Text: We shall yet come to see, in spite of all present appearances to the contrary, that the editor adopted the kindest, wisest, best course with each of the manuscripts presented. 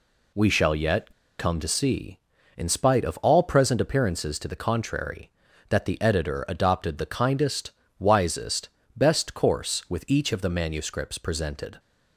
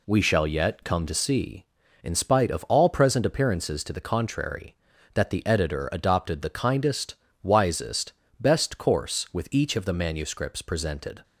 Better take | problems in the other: second | pauses between "yet" and "come"; slight; at 1.1 s; 0.28 s long

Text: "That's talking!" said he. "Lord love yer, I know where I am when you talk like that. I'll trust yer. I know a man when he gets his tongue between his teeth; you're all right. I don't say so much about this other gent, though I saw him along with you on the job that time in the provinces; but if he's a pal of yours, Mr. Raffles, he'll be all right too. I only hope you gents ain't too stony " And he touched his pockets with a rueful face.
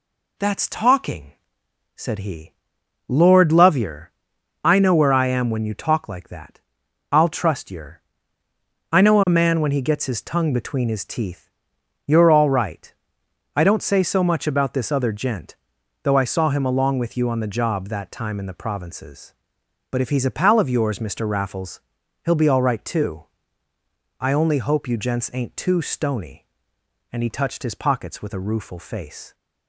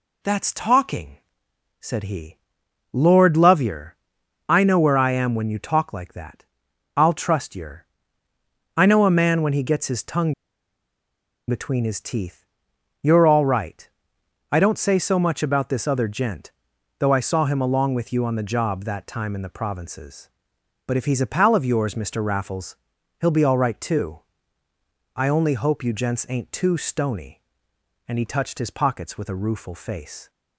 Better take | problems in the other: first | pauses between "tongue" and "between"; at 10.3 s; 1.1 s long

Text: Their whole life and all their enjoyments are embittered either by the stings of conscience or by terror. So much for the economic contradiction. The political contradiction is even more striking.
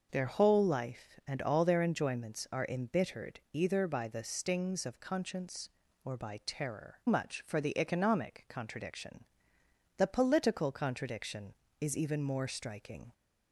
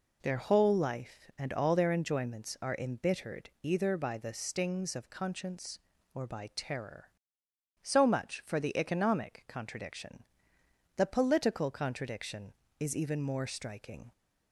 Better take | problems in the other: second | skips "So"; at 7.0 s

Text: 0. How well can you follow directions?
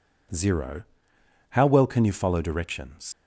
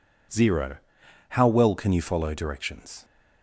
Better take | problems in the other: second | leaves "directions" unfinished; at 3.1 s; 95 ms

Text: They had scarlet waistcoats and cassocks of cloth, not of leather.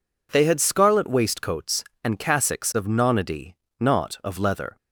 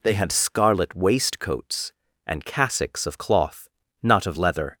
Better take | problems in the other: second | says "nonody" for "cloth"; at 2.8 s

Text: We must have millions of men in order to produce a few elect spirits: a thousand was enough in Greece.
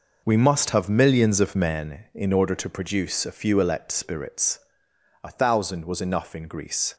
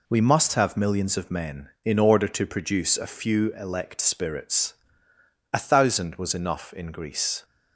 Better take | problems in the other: second | starts louder than the rest; noticeable; until 1.9 s; 5.5 dB

